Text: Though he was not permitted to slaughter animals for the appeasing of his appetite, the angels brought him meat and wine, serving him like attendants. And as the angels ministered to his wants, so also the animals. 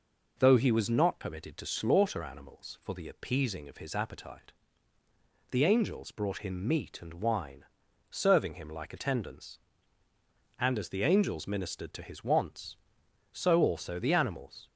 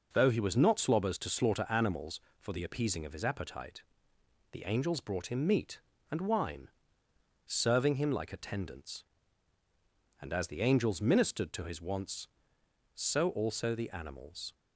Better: first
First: none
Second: says "slobbers" for "permitted"; at 0.7 s

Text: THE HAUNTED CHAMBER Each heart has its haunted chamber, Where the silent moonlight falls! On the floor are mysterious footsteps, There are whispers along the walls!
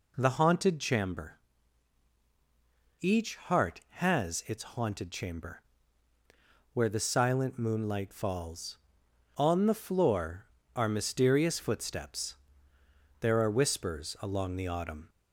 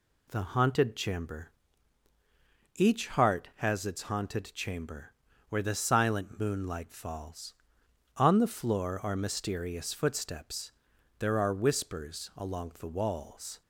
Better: second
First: pauses between "CHAMBER" and "Each"; strong; at 1.3 s; 1.6 s long // says "autumn" for "walls"; at 14.6 s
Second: pauses between "CHAMBER" and "Each"; at 1.5 s; 1.2 s long

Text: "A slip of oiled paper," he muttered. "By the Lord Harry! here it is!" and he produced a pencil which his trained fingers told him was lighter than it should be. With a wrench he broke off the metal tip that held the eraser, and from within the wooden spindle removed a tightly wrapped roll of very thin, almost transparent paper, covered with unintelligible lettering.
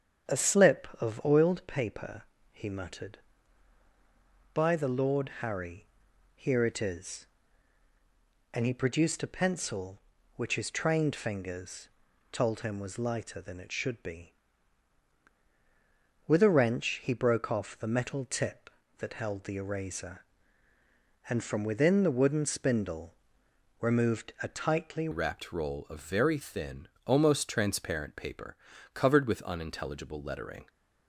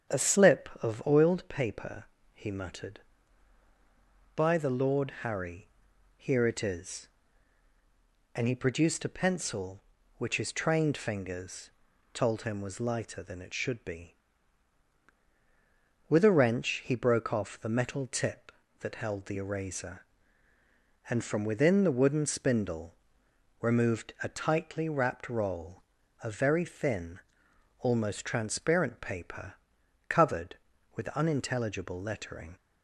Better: second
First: starts louder than the rest; strong; until 1.4 s; 8.5 dB // pauses between "fingers" and "told"; at 11.8 s; 0.42 s long // pauses between "spindle" and "removed"; noticeable; at 23.1 s; 0.68 s long // changes voice at "wrapped"; from 25.1 s on; 5.5 s long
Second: starts louder than the rest; strong; until 1.2 s; 8.5 dB // pauses between "fingers" and "told"; at 11.7 s; 0.42 s long // pauses between "spindle" and "removed"; noticeable; at 22.9 s; 0.68 s long

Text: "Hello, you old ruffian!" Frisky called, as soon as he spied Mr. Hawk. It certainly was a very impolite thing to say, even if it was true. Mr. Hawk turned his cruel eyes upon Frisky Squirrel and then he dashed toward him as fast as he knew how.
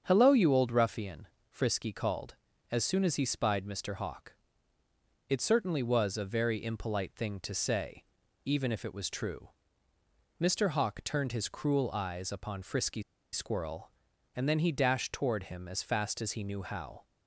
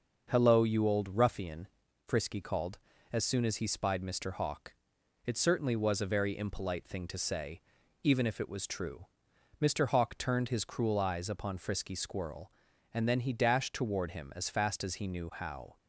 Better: second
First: starts louder than the rest; strong; until 1.0 s; 7 dB // pauses between "Frisky" and "Squirrel"; slight; at 13.0 s; 0.30 s long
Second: starts louder than the rest; until 1.3 s; 6 dB

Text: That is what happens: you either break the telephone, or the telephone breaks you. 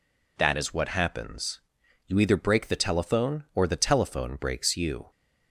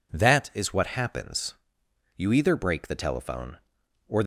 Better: first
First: none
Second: stops before "the telephone breaks you"; at 4.2 s

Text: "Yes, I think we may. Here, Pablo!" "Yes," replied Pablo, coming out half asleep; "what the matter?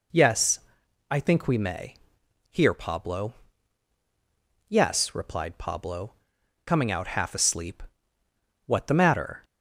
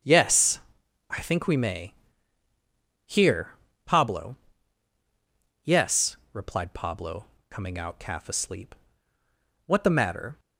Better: first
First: none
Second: starts louder than the rest; strong; until 1.5 s; 8 dB // says "calf" for "half"; at 8.0 s

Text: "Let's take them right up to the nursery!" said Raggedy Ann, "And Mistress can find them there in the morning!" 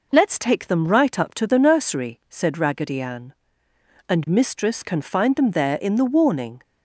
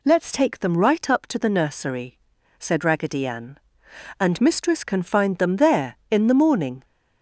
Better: second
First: says "warning" for "morning"; at 6.0 s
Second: none

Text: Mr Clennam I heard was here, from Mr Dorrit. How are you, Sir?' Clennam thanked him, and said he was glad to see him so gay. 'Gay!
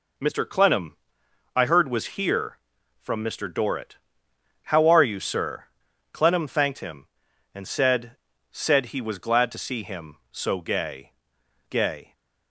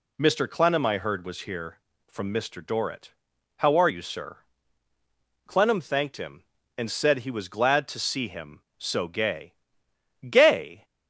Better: second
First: pauses between "Clennam" and "I"; noticeable; at 0.9 s; 0.58 s long // says "said" twice; at 8.5 s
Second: none

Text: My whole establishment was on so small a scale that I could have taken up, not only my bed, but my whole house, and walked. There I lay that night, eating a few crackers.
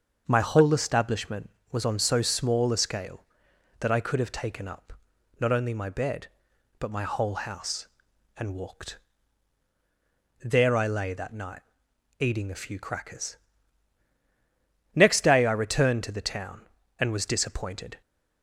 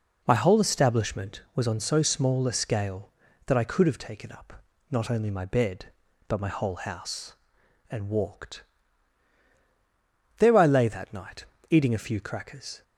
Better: second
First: starts louder than the rest; until 1.3 s; 6.5 dB // goes on to say "Next day I returned to the town and was disappointed"; strong; from 14.9 s on; 3.0 s long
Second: none

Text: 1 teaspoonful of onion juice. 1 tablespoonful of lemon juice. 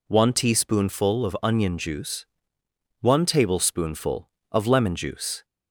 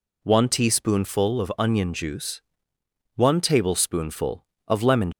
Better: first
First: none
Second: stops before "juice"; at 5.1 s

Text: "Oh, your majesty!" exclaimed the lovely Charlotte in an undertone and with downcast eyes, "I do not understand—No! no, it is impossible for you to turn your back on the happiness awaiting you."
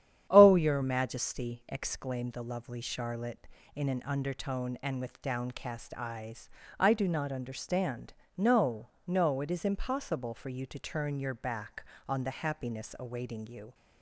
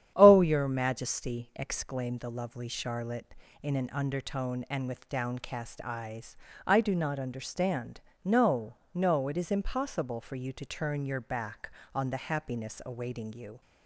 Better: neither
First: starts louder than the rest; strong; until 1.3 s; 9.5 dB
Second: starts louder than the rest; strong; until 1.1 s; 9.5 dB

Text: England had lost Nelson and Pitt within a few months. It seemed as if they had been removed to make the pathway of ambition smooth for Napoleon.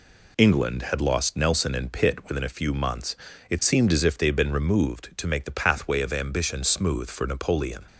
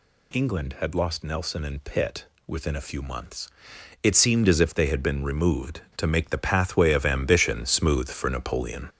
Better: first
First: none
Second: gets louder; throughout; 6.5 dB // pauses between "Pitt" and "within"; slight; at 2.2 s; 0.22 s long

